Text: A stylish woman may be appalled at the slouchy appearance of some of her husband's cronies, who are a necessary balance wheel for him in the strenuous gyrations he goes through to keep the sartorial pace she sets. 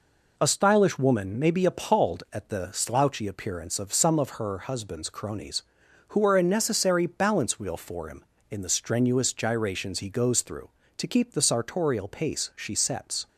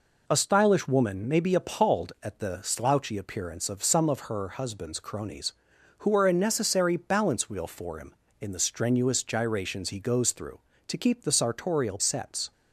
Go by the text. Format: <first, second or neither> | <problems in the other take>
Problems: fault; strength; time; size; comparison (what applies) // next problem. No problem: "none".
first | skips "pace she"; at 11.9 s